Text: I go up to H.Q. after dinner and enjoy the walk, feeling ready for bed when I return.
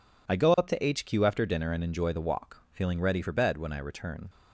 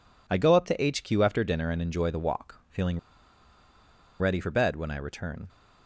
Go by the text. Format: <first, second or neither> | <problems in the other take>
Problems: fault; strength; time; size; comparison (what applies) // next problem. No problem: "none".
first | pauses between "feeling" and "ready"; at 2.9 s; 1.2 s long